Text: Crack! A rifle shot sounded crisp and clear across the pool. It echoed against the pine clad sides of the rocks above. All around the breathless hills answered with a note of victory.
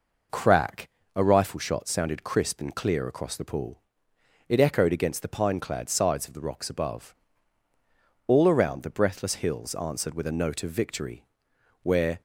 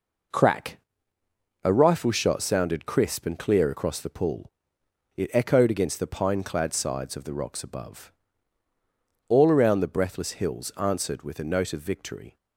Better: second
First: goes on to say "Where"; slight; from 11.8 s on; 0.38 s long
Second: none

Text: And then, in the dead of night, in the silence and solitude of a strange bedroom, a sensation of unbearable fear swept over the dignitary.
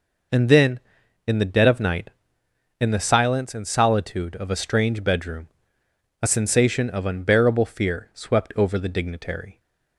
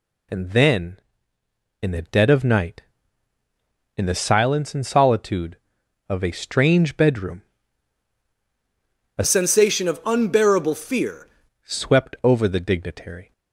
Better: first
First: none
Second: changes voice from "sensation" to "fear"; from 9.2 to 11.2 s; 2.0 s long

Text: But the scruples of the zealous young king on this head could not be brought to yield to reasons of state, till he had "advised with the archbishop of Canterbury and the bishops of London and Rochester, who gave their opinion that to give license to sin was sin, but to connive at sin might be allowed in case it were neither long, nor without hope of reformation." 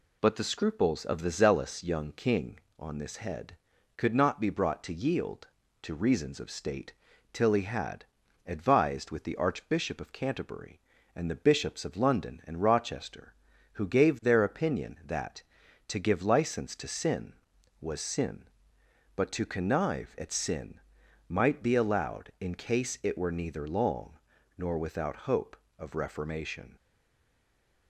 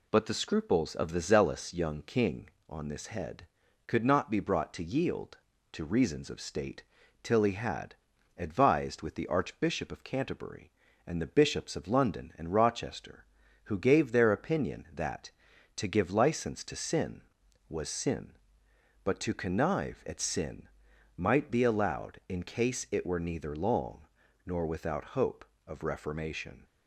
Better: second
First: pauses between "had" and "advised"; at 8.0 s; 0.42 s long // pauses between "sin" and "might"; noticeable; at 20.7 s; 0.48 s long // stays silent after the last word; from 26.7 s on; 1.1 s long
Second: pauses between "had" and "advised"; at 7.9 s; 0.43 s long // pauses between "sin" and "might"; noticeable; at 20.6 s; 0.48 s long

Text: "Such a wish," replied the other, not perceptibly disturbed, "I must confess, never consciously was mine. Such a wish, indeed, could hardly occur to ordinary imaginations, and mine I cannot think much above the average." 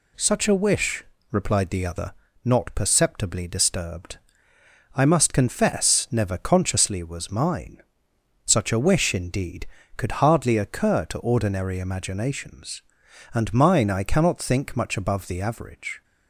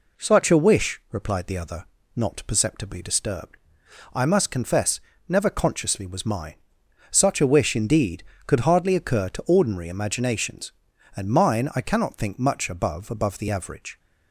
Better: first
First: none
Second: says "above" twice; at 13.0 s

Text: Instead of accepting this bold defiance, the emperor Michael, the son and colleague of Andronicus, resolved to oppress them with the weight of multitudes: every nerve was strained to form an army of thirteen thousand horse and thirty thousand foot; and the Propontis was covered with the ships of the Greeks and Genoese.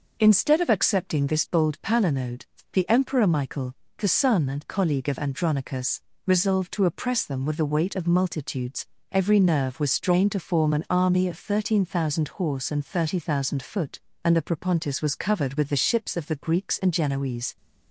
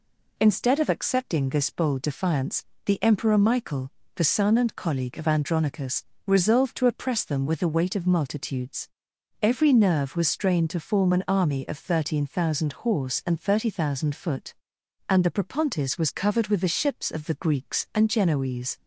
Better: second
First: says "palinode" for "defiance"; at 1.8 s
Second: none

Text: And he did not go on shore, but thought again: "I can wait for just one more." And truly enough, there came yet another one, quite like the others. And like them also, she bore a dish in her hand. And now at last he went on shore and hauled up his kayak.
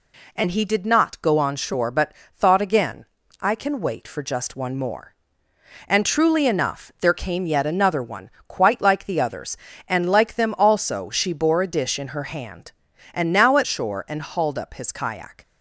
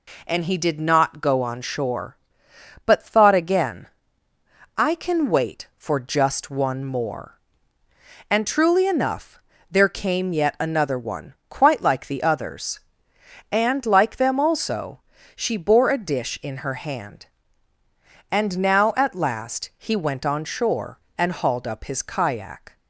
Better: second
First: pauses between "but" and "thought"; slight; at 2.1 s; 0.24 s long // skips "last he went on"; at 13.6 s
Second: none

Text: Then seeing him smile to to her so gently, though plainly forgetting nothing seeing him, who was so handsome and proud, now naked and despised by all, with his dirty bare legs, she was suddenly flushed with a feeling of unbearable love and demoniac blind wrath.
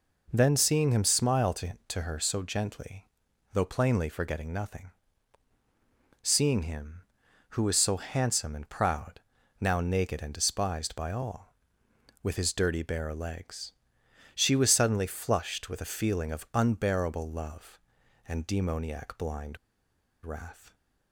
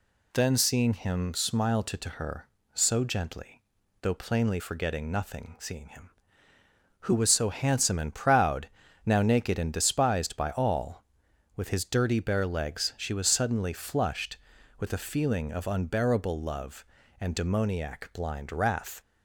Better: second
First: pauses between "nothing" and "seeing"; strong; at 4.9 s; 1.3 s long // pauses between "blind" and "wrath"; noticeable; at 19.5 s; 0.66 s long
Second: none

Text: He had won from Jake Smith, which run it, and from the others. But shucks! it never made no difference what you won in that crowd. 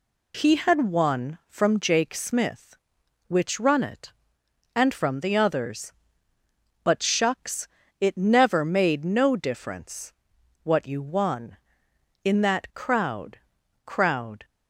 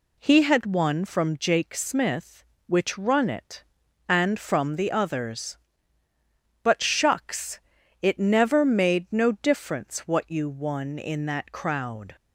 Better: second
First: pauses between "difference" and "what"; noticeable; at 10.1 s; 0.52 s long // says "crowd" twice; at 13.8 s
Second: none

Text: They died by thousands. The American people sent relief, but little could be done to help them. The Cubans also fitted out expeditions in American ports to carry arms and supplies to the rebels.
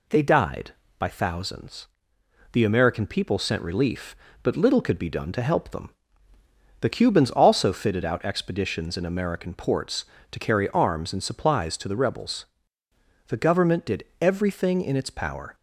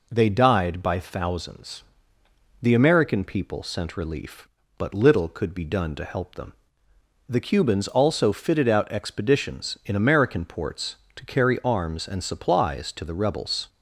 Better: second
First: goes on to say "The government did everything in its power"; strong; from 13.2 s on; 2.2 s long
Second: none

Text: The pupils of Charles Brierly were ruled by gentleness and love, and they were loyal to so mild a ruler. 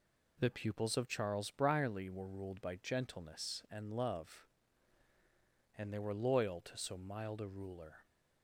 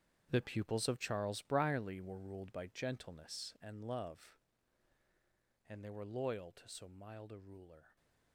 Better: first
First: none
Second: gets quieter; strong; throughout; 13 dB

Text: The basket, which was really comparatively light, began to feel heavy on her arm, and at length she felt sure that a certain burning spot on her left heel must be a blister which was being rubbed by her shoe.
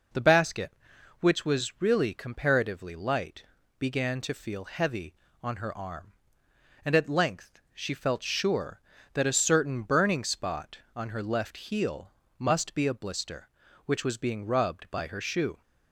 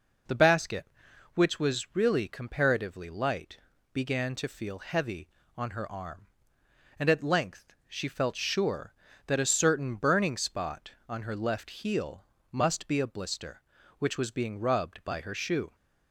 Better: neither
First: pauses between "heel" and "must"; slight; at 12.1 s; 0.26 s long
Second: pauses between "heel" and "must"; slight; at 12.2 s; 0.26 s long

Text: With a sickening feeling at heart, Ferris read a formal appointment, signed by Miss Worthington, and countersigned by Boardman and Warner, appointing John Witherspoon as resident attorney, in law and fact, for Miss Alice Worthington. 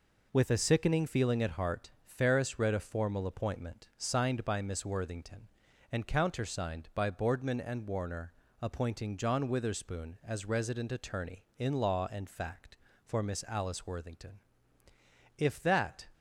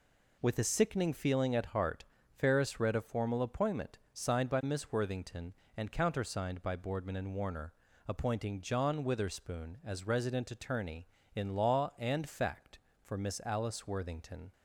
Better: second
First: goes on to say "If that"; noticeable; from 15.3 s on; 0.70 s long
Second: none

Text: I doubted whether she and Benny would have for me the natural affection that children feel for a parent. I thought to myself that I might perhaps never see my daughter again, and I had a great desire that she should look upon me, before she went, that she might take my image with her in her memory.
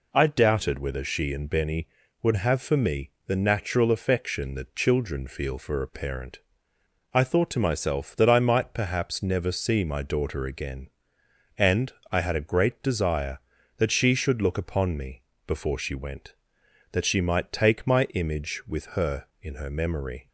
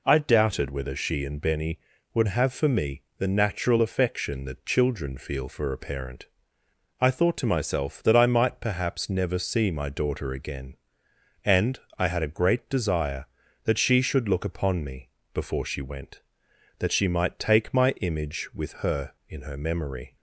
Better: neither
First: pauses between "me" and "the"; slight; at 3.1 s; 0.16 s long // pauses between "and" and "I"; slight; at 11.9 s; 0.18 s long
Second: pauses between "me" and "the"; slight; at 3.0 s; 0.16 s long // pauses between "and" and "I"; slight; at 11.7 s; 0.18 s long

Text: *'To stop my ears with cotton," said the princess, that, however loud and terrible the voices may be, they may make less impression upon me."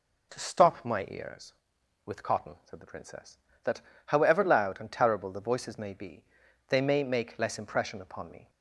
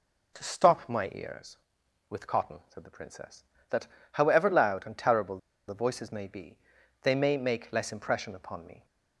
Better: first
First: none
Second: pauses between "terrible" and "the"; slight; at 5.3 s; 0.30 s long

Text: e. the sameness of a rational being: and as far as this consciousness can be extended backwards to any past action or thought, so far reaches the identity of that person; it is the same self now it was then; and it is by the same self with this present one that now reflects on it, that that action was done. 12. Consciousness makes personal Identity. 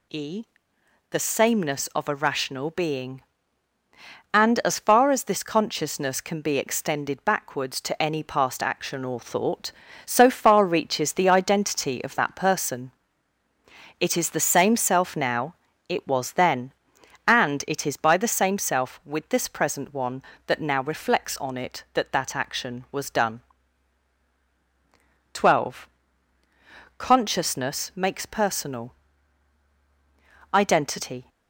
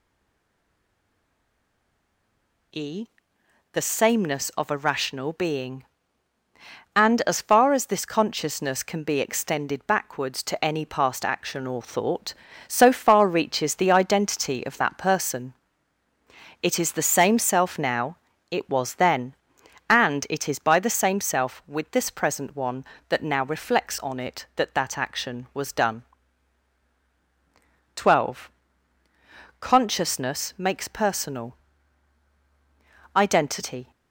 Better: first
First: pauses between "now" and "it"; slight; at 15.5 s; 0.36 s long // pauses between "personal" and "Identity"; strong; at 28.9 s; 1.5 s long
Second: stays silent before the first word; strong; until 2.7 s; 2.7 s long // pauses between "now" and "it"; slight; at 18.1 s; 0.36 s long // pauses between "personal" and "Identity"; strong; at 31.5 s; 1.5 s long

